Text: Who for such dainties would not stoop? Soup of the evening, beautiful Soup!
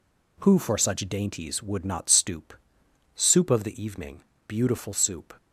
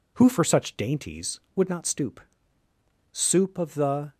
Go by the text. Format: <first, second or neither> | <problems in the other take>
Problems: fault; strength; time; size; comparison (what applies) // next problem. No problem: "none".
first | stops before "evening beautiful Soup"; at 4.1 s